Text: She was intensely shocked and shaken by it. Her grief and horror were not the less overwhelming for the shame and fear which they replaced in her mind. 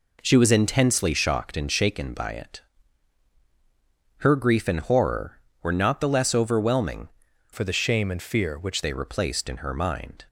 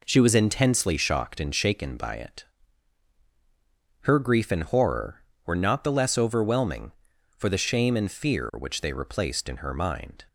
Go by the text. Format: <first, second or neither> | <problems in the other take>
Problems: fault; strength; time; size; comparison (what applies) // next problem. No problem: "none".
second | changes voice from "for" to "which"; from 7.5 to 8.8 s; 1.3 s long